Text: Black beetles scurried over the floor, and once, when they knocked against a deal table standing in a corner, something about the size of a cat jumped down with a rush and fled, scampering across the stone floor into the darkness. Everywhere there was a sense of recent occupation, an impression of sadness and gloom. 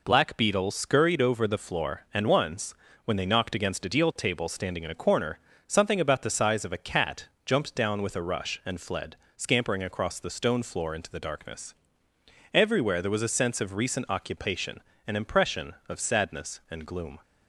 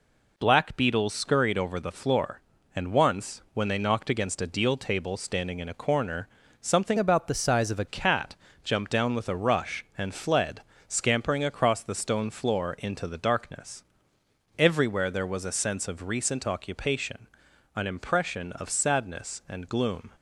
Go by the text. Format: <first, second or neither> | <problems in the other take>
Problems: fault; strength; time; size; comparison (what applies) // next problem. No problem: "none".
first | changes voice from "about" to "a"; from 6.9 to 7.8 s; 0.9 s long // pauses between "cat" and "jumped"; slight; at 8.3 s; 0.26 s long; slight in the first